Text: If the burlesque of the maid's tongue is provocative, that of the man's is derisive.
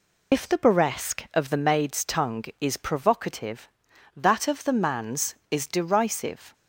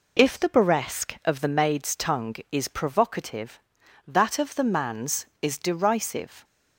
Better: second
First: loses the start of "If"; at 0.3 s; 60 ms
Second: none

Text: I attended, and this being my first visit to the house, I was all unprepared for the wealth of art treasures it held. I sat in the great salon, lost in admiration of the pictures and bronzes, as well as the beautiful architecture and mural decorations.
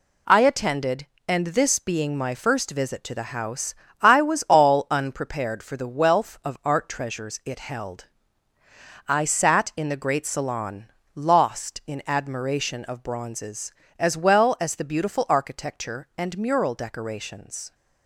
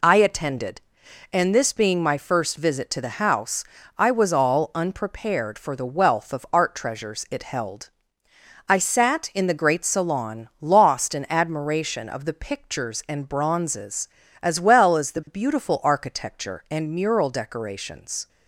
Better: second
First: skips "the pictures and"; at 13.0 s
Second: none

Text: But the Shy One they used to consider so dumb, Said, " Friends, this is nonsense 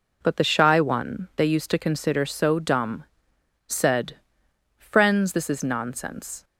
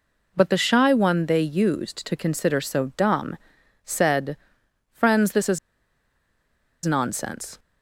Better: first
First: none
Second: pauses between "is" and "nonsense"; strong; at 5.5 s; 1.2 s long

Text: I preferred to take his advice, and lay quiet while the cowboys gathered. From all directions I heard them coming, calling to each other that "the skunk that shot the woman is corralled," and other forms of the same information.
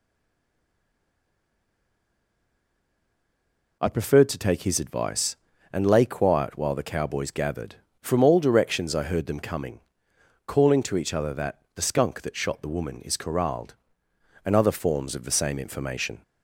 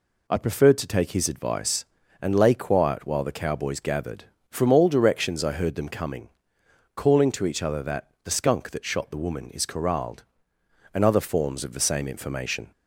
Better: second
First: stays silent before the first word; strong; until 3.8 s; 3.8 s long // pauses between "that" and "the"; slight; at 11.6 s; 0.16 s long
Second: pauses between "that" and "the"; slight; at 8.0 s; 0.16 s long

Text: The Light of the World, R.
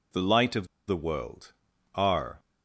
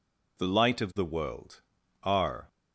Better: second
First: pauses between "of" and "the"; slight; at 0.6 s; 0.21 s long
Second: none

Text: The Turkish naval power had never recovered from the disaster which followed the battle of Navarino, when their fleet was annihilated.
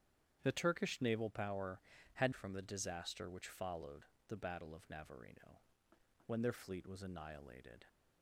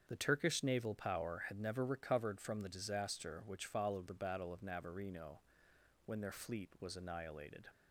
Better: second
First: starts louder than the rest; strong; until 1.4 s; 9 dB // skips "never recovered"; at 2.3 s // pauses between "followed" and "the"; slight; at 4.0 s; 0.24 s long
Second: starts louder than the rest; strong; until 1.0 s; 7 dB

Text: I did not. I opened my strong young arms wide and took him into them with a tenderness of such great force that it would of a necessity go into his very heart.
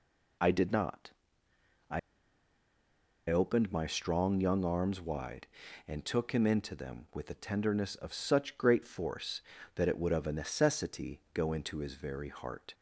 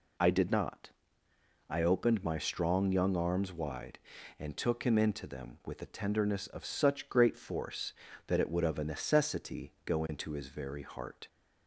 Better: second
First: pauses between "I" and "opened"; strong; at 1.9 s; 1.2 s long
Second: none

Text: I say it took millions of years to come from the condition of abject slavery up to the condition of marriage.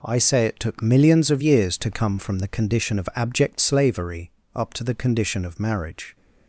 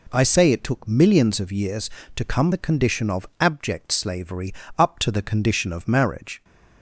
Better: first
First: pauses between "slavery" and "up"; slight; at 4.3 s; 0.24 s long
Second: skips "from"; at 2.5 s // pauses between "slavery" and "up"; slight; at 4.5 s; 0.24 s long

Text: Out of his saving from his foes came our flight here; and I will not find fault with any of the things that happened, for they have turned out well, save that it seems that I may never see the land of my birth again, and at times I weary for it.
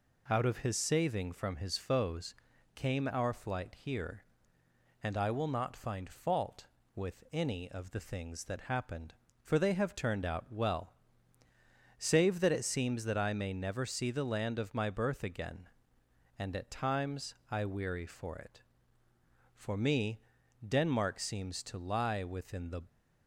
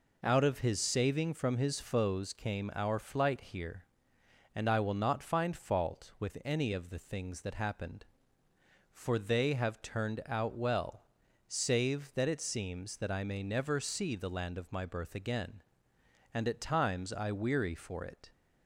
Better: second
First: pauses between "foes" and "came"; at 2.3 s; 0.40 s long // goes on to say "For me Denmark seems to lie within the"; strong; from 19.5 s on; 3.2 s long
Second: none

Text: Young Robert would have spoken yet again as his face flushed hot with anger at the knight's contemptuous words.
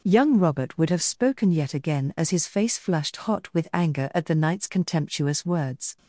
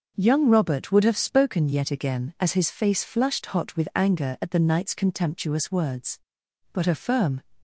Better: first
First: none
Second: starts louder than the rest; noticeable; until 1.2 s; 6 dB // goes on to say "But a firm"; noticeable; from 6.7 s on; 0.70 s long

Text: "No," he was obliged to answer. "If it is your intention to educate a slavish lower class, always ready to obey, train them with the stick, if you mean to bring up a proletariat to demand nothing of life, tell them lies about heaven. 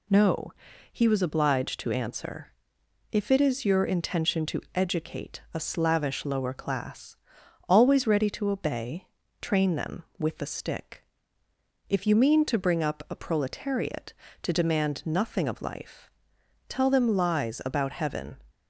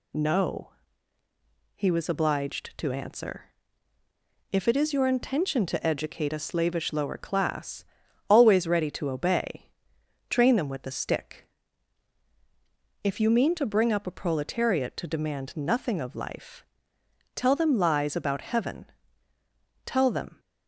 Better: first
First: none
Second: goes on to say "Tell them"; from 19.8 s on; 0.54 s long

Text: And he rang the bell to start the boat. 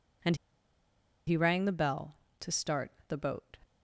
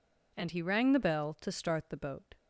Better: second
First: pauses between "And" and "he"; noticeable; at 0.3 s; 0.91 s long // pauses between "start" and "the"; slight; at 2.9 s; 0.16 s long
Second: none

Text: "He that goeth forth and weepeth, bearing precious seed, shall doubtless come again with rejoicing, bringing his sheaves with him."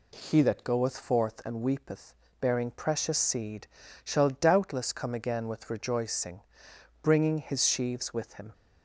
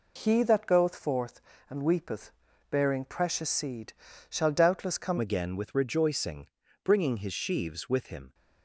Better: first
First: none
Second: changes voice at "again"; from 5.1 s on; 3.2 s long

